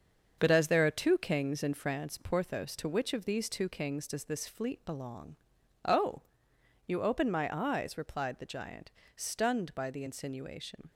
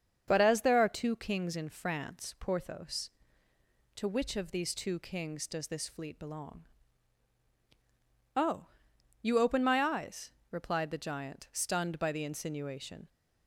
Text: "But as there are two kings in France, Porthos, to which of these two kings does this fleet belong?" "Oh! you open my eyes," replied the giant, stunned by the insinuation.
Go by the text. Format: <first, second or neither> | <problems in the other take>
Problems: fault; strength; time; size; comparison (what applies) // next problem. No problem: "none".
second | gets quieter; throughout; 6.5 dB // starts louder than the rest; until 1.4 s; 7 dB; strong in the second